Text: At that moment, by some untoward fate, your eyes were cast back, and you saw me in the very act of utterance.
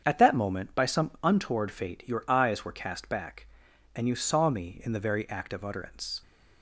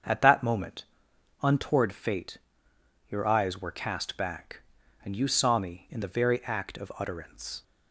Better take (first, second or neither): first